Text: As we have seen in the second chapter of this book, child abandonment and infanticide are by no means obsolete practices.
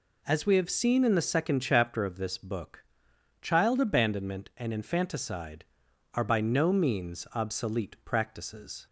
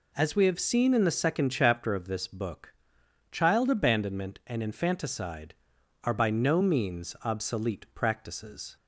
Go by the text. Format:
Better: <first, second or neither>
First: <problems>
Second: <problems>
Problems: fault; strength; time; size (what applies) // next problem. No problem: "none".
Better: neither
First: none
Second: none